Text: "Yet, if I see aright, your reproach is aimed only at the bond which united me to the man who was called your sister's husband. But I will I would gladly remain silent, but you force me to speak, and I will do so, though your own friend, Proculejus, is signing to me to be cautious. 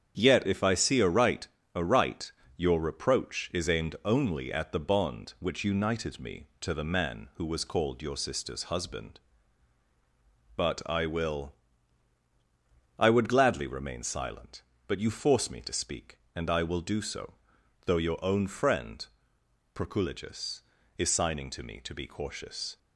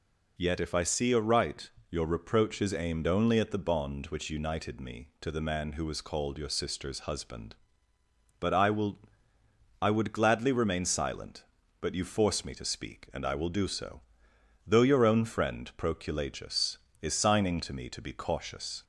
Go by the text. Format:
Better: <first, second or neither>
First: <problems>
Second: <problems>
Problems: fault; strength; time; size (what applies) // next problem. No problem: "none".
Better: second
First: starts louder than the rest; strong; until 1.1 s; 8 dB // says "aright" twice; at 1.7 s // pauses between "will" and "I"; strong; at 11.5 s; 1.4 s long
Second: pauses between "will" and "I"; noticeable; at 8.9 s; 0.82 s long